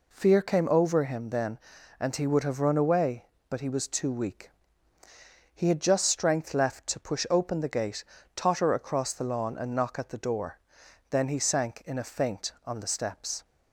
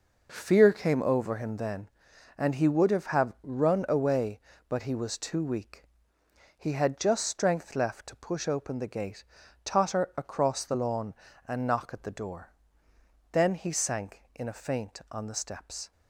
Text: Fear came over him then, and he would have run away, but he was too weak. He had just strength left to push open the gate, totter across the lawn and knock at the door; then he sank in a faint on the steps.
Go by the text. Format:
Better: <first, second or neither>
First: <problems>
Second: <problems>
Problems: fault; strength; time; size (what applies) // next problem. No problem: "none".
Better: first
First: none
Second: says "have" twice; at 3.0 s